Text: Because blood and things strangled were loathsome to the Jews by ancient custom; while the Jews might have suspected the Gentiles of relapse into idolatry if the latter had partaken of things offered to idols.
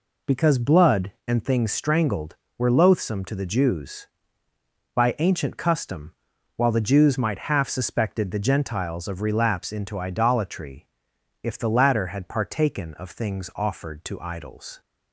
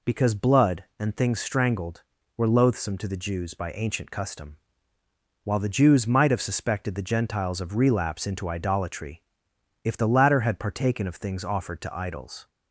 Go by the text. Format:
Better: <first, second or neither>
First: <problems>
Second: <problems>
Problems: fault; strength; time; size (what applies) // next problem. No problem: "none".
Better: second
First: says "half" for "have"; at 7.5 s // pauses between "idolatry" and "if"; noticeable; at 10.8 s; 0.56 s long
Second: pauses between "idolatry" and "if"; noticeable; at 9.2 s; 0.62 s long